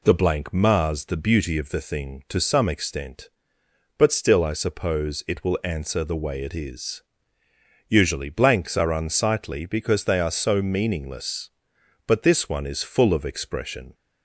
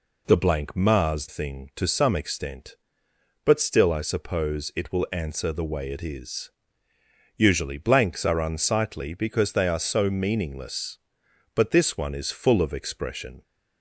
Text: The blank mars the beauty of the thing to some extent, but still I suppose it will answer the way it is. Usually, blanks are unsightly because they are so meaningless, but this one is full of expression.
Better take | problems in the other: first | skips "the beauty of the"; at 1.2 s

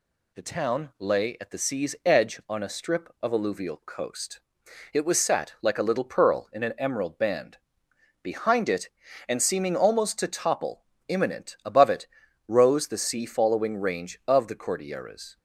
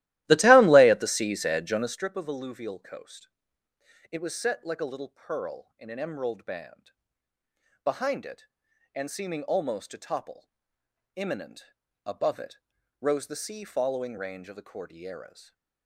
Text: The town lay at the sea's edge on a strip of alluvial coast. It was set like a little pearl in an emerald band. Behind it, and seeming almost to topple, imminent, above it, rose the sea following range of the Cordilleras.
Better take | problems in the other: first | starts louder than the rest; strong; until 2.1 s; 15.5 dB

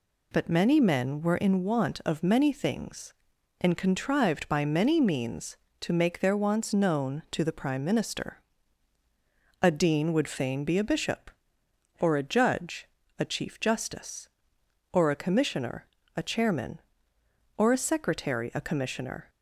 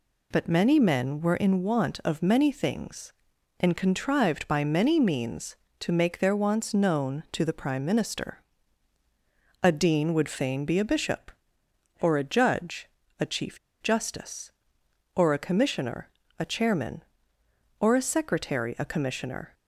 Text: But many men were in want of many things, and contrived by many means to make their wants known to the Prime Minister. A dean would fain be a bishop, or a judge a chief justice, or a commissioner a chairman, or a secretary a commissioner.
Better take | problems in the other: first | pauses between "judge" and "a"; slight; at 12.8 s; 0.32 s long; slight in the first // pauses between "chief" and "justice"; slight; at 13.5 s; 0.22 s long // pauses between "commissioner" and "a"; slight; at 16.0 s; 0.32 s long; slight in the first

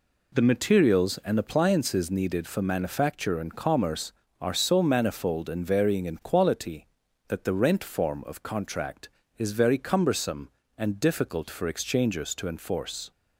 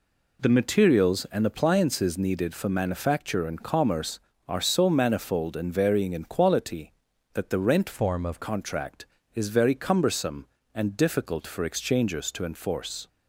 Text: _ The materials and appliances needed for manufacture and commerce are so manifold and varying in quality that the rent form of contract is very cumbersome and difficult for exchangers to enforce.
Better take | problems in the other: first | changes voice from "form" to "of"; from 7.9 to 8.4 s; 0.5 s long

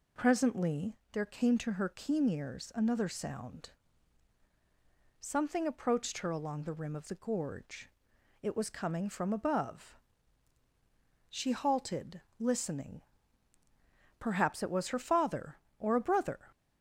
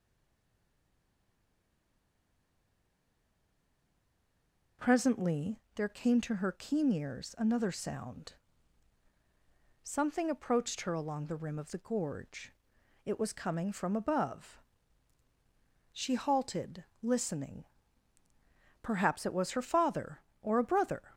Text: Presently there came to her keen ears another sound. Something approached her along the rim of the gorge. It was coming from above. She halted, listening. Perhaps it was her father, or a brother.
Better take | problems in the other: first | stays silent before the first word; strong; until 4.7 s; 4.7 s long // pauses between "Presently" and "there"; slight; at 5.5 s; 0.16 s long; slight in the first

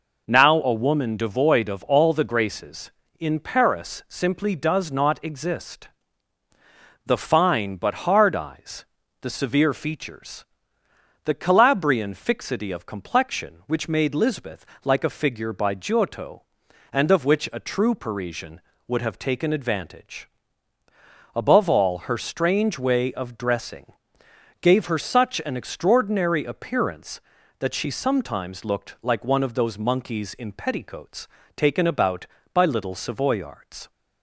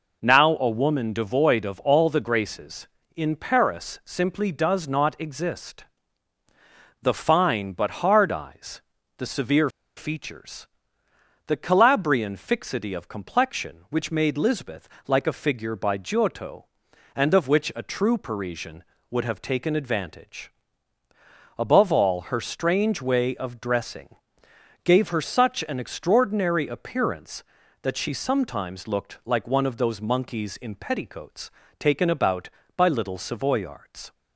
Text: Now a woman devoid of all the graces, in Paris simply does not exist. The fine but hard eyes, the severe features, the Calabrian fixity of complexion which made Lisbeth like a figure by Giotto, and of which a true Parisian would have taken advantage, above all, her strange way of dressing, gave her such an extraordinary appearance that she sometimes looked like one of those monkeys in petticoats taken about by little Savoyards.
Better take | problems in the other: first | pauses between "severe" and "features"; slight; at 9.6 s; 0.26 s long // pauses between "Lisbeth" and "like"; slight; at 14.8 s; 0.22 s long; slight in the first // pauses between "petticoats" and "taken"; slight; at 31.4 s; 0.28 s long; slight in the first

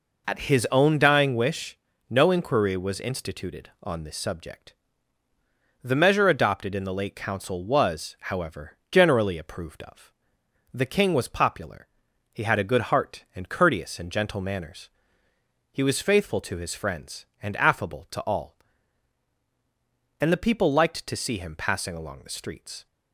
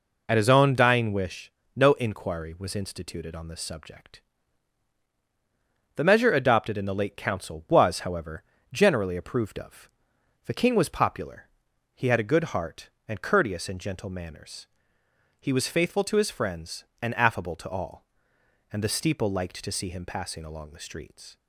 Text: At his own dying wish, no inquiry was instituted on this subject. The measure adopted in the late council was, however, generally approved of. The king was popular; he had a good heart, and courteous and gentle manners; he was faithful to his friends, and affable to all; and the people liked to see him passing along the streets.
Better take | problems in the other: first | says "steeple" for "people"; at 18.8 s

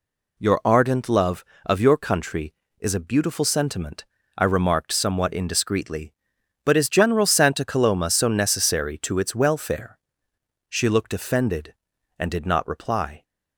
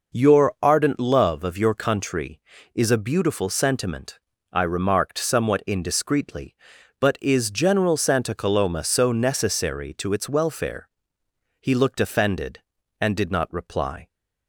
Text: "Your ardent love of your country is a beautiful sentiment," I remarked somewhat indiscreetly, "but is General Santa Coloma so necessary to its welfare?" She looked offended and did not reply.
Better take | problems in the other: first | says "He" for "She"; at 11.5 s

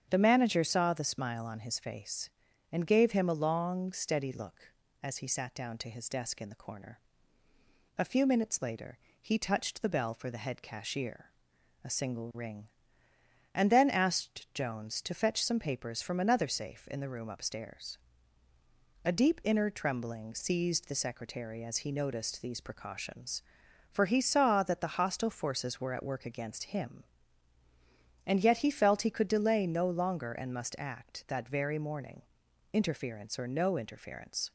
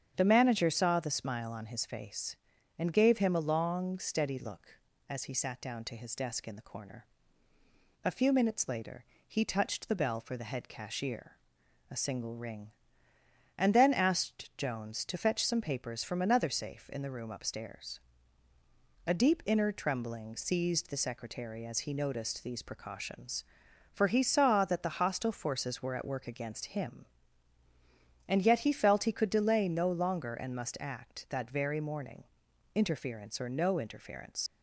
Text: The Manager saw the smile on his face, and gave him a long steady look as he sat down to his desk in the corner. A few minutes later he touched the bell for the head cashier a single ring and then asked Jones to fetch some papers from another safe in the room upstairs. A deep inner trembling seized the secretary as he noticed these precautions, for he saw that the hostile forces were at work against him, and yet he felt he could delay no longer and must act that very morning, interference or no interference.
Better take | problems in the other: first | starts louder than the rest; strong; until 1.1 s; 8 dB; strong in the first // pauses between "later" and "he"; slight; at 9.0 s; 0.24 s long; slight in the first // pauses between "cashier" and "a"; noticeable; at 11.3 s; 0.54 s long; noticeable in the first // leaves "interference" unfinished; at 34.4 s; 75 ms

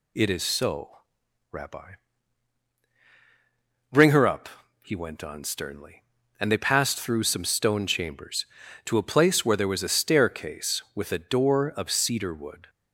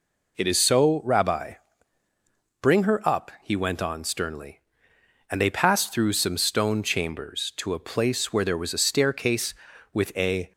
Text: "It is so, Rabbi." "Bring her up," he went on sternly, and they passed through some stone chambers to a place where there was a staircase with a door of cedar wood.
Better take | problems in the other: first | stops before "door of cedar wood"; at 10.5 s

